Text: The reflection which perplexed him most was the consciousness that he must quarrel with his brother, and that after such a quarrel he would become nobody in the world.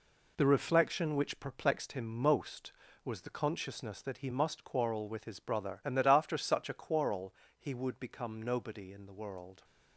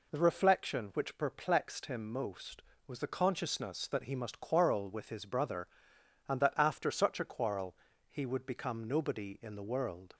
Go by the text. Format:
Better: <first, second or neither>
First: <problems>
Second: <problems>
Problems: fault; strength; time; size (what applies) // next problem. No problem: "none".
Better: second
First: gets quieter; strong; throughout; 7.5 dB // pauses between "quarrel" and "he"; slight; at 7.3 s; 0.26 s long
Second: pauses between "quarrel" and "he"; slight; at 7.7 s; 0.34 s long